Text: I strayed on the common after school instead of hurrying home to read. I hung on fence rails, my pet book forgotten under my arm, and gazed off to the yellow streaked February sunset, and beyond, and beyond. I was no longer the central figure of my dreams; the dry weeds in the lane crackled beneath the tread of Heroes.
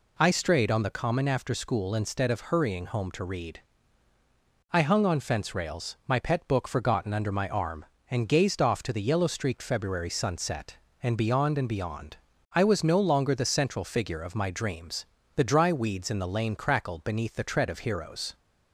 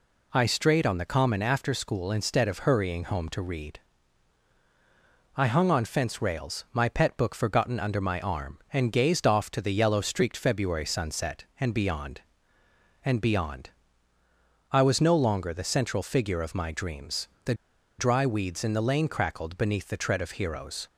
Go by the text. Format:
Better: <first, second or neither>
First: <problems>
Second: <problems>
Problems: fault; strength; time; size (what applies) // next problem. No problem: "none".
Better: first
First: none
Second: pauses between "the" and "dry"; at 17.5 s; 0.44 s long